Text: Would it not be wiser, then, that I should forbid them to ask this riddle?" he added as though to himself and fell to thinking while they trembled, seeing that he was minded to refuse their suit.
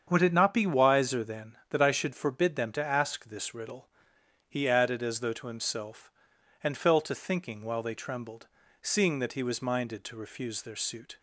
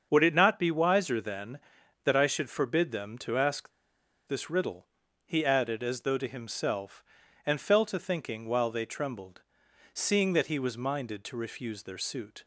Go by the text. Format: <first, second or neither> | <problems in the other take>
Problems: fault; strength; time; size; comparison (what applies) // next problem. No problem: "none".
first | starts louder than the rest; until 1.1 s; 7 dB; strong in the first // pauses between "ask" and "this"; noticeable; at 3.7 s; 0.57 s long